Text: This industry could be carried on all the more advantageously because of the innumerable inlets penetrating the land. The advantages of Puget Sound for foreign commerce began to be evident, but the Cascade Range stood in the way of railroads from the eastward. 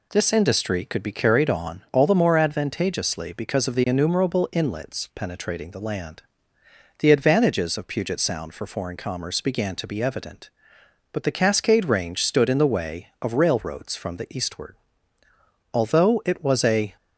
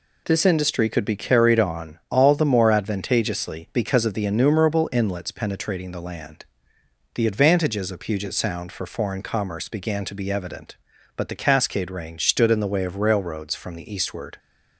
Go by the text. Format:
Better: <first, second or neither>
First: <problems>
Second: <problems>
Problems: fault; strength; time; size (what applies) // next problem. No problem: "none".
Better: second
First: goes on to say "Although it was a"; noticeable; from 15.7 s on; 1.2 s long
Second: none